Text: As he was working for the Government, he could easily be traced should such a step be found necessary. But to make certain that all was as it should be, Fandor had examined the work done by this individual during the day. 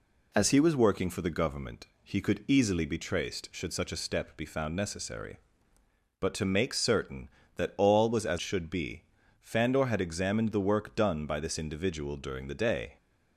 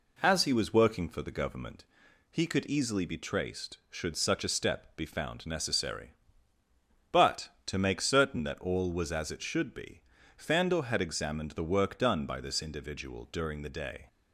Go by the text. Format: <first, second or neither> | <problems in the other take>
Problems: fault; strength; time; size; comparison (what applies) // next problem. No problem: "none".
second | skips "it"; at 8.3 s